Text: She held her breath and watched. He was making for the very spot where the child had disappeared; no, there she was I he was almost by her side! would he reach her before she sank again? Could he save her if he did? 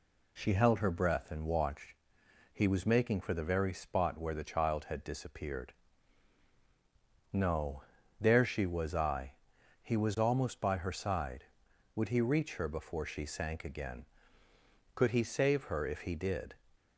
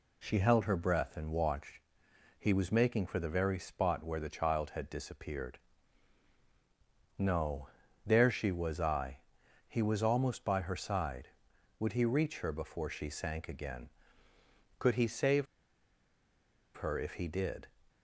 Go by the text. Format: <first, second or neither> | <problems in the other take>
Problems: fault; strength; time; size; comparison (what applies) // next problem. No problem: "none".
first | pauses between "I" and "he"; noticeable; at 9.1 s; 0.50 s long; noticeable in the first // pauses between "save" and "her"; strong; at 15.4 s; 1.3 s long